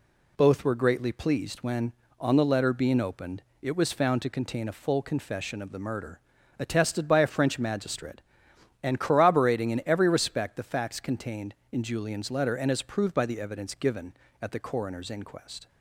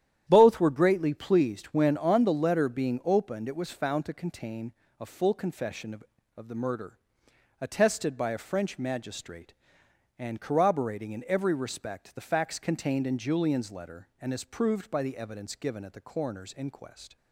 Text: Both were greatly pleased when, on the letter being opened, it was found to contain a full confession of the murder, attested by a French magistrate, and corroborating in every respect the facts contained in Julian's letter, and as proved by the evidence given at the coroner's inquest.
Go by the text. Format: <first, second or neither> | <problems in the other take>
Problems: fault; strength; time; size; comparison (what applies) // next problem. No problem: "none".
first | starts louder than the rest; strong; until 1.2 s; 10.5 dB // pauses between "contain" and "a"; slight; at 4.7 s; 0.26 s long // says "of" twice; at 6.3 s